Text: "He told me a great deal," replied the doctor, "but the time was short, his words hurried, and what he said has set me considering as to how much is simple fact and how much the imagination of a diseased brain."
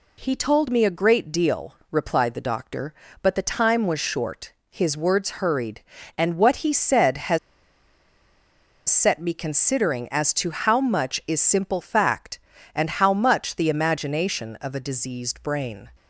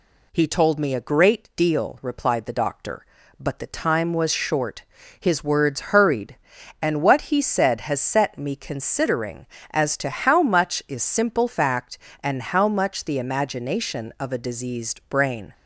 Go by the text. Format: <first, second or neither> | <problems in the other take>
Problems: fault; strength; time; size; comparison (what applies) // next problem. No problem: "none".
second | pauses between "has" and "set"; strong; at 7.3 s; 1.5 s long